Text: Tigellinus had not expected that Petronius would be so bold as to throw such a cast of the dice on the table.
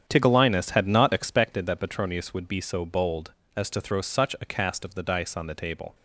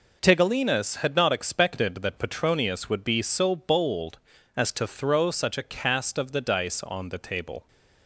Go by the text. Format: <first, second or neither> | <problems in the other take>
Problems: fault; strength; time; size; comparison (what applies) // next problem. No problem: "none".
second | starts louder than the rest; strong; until 1.5 s; 8.5 dB